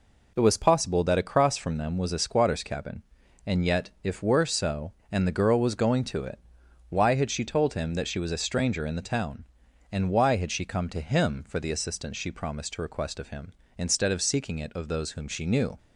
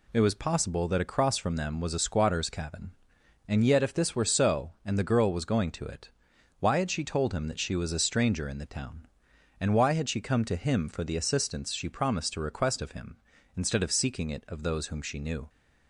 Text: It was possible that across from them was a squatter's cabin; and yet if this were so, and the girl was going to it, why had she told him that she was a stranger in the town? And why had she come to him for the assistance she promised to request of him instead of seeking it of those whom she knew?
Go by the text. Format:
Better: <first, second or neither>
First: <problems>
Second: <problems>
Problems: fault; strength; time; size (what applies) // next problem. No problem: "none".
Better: second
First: skips "this"; at 4.2 s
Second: none